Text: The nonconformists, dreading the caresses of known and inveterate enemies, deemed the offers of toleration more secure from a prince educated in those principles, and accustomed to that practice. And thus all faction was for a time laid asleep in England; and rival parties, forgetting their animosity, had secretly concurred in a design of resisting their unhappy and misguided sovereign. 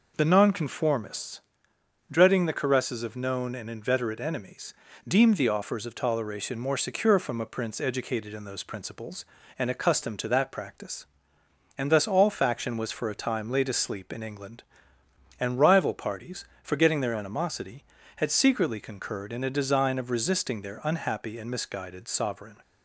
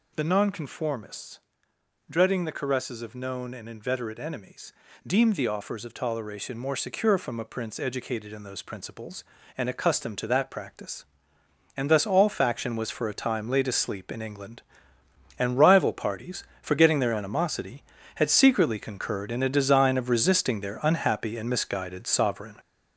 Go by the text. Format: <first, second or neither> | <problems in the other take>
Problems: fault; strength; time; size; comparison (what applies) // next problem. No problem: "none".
first | gets louder; noticeable; throughout; 6 dB